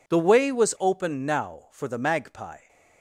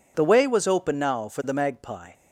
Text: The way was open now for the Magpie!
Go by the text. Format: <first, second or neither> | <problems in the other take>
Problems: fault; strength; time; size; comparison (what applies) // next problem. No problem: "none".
neither | none